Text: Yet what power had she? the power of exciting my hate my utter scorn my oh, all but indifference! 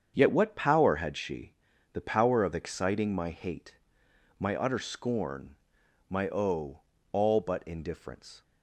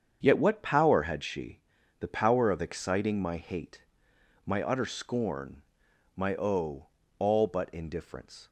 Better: neither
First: starts louder than the rest; strong; until 1.1 s; 7.5 dB // pauses between "hate" and "my"; noticeable; at 3.7 s; 0.64 s long // pauses between "scorn" and "my"; noticeable; at 5.5 s; 0.54 s long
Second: starts louder than the rest; strong; until 1.2 s; 7.5 dB // pauses between "hate" and "my"; noticeable; at 3.8 s; 0.64 s long // pauses between "scorn" and "my"; noticeable; at 5.6 s; 0.54 s long

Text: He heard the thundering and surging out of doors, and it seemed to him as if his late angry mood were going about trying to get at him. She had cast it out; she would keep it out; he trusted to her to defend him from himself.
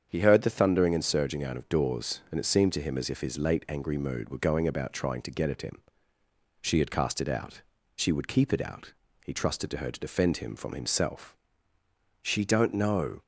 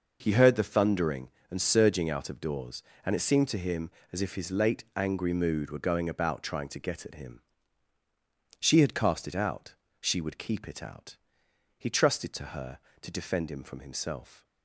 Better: second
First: starts louder than the rest; strong; until 1.1 s; 7.5 dB // goes on to say "She don't know"; noticeable; from 12.2 s on; 0.98 s long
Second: none

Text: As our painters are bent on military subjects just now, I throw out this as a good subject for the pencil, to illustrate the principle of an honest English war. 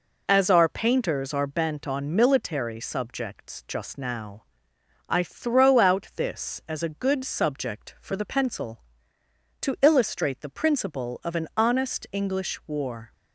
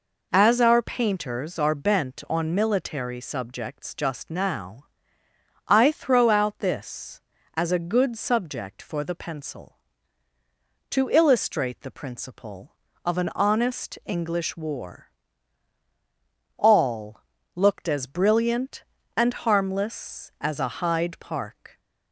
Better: first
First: none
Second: goes on to say "All looked as brilliant and harmless as a Hyde Park"; strong; from 16.5 s on; 5.2 s long

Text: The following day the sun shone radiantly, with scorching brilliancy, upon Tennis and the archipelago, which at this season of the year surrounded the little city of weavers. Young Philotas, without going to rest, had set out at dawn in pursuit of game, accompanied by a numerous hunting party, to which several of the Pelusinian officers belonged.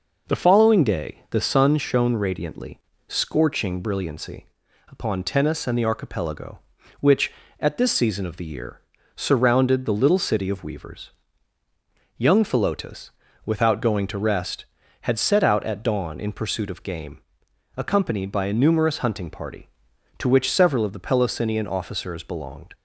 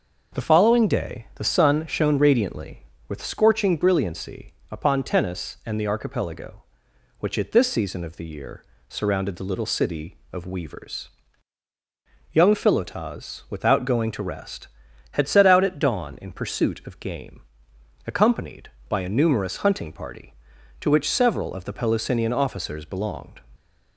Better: second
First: skips "with"; at 2.9 s // pauses between "year" and "surrounded"; slight; at 8.8 s; 0.34 s long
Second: pauses between "year" and "surrounded"; slight; at 8.6 s; 0.24 s long

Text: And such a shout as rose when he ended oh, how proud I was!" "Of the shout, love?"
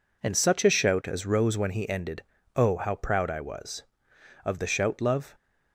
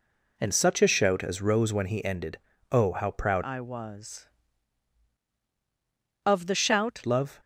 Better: first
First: pauses between "ended" and "oh"; slight; at 2.2 s; 0.32 s long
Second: pauses between "ended" and "oh"; slight; at 2.3 s; 0.32 s long // changes voice from "I" to "shout"; from 3.4 to 7.0 s; 3.6 s long

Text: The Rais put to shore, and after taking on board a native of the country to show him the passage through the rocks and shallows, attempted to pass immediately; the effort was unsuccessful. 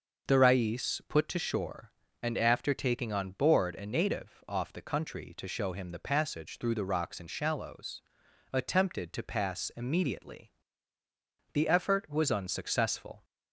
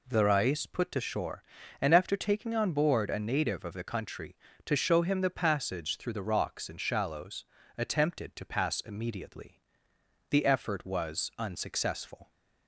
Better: second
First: starts louder than the rest; until 1.3 s; 6.5 dB // says "off" for "of"; at 4.4 s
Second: none

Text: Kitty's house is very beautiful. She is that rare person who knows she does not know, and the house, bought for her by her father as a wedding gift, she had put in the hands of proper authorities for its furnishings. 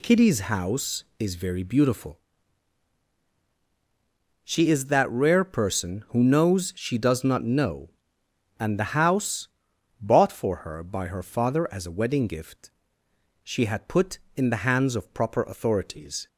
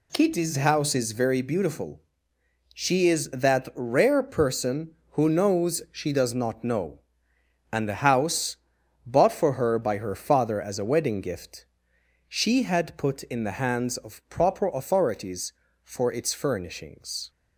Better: second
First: stops before "for its furnishings"; at 16.2 s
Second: none

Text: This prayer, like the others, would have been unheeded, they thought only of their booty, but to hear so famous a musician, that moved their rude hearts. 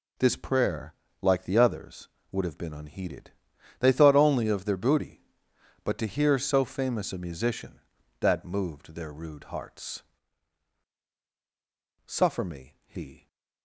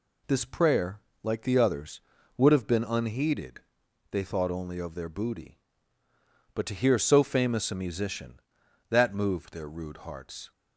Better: second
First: goes on to say "Suffer me he"; noticeable; from 12.0 s on; 1.2 s long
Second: none

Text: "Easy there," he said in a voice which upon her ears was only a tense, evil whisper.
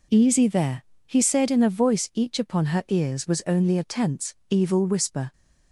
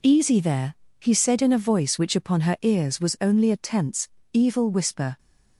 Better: second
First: says "each" for "which"; at 2.1 s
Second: none

